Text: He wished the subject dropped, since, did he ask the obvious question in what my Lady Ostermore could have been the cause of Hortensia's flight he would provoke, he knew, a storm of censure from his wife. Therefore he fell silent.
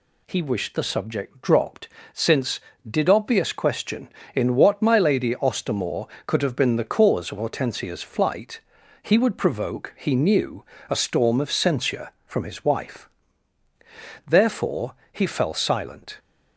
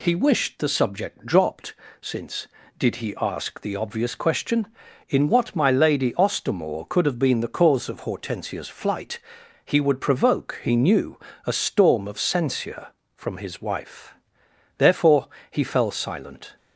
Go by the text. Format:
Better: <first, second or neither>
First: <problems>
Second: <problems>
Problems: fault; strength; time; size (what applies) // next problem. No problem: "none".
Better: second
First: skips "he ask the"; at 3.0 s // pauses between "flight" and "he"; at 8.6 s; 0.44 s long // pauses between "Therefore" and "he"; slight; at 14.9 s; 0.16 s long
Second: pauses between "flight" and "he"; at 9.1 s; 0.44 s long // pauses between "Therefore" and "he"; slight; at 15.2 s; 0.24 s long